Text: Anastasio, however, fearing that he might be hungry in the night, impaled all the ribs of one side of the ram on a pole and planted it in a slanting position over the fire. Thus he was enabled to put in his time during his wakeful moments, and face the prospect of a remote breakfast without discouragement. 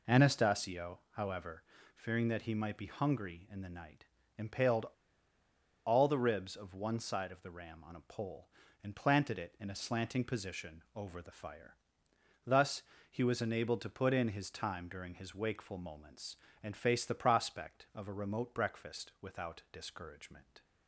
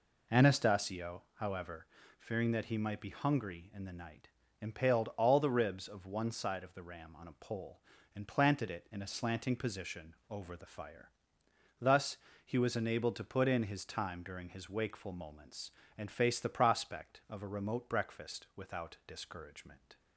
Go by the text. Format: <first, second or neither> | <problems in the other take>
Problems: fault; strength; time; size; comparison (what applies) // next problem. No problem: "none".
second | pauses between "impaled" and "all"; at 4.8 s; 1.0 s long // pauses between "Thus" and "he"; slight; at 12.8 s; 0.26 s long; slight in the second